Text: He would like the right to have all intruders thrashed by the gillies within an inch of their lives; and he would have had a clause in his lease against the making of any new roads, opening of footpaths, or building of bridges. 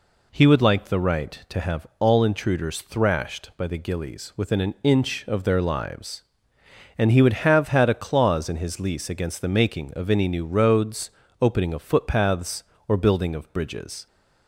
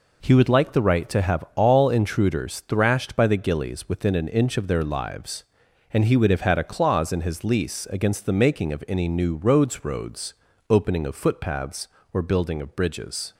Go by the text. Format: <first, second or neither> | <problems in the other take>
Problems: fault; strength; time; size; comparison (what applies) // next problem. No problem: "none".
first | says "roads" twice; at 9.8 s